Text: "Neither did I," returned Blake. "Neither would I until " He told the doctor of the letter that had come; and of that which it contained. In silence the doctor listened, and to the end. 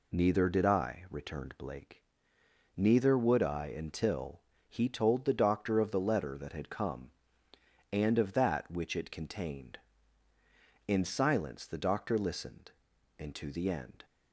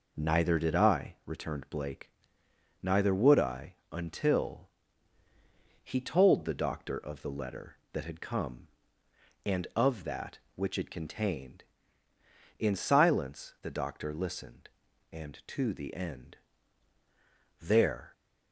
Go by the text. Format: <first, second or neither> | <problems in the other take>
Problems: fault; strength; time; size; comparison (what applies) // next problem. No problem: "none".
first | pauses between "I" and "until"; slight; at 3.7 s; 0.16 s long // goes on to say "There"; from 17.6 s on; 0.52 s long